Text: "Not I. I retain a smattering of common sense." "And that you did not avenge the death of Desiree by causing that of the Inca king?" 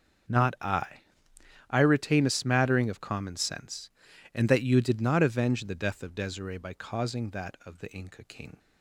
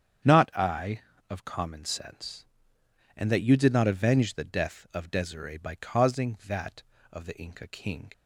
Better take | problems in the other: first | starts louder than the rest; strong; until 1.5 s; 8 dB; also in the first // skips "I retain a smattering"; at 1.1 s

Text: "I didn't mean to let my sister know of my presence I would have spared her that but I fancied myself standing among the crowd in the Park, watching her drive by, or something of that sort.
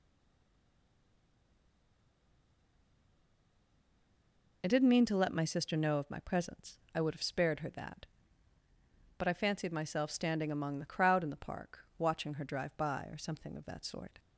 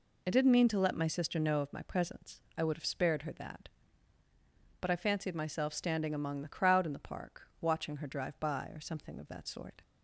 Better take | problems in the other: second | stays silent before the first word; strong; until 4.6 s; 4.6 s long

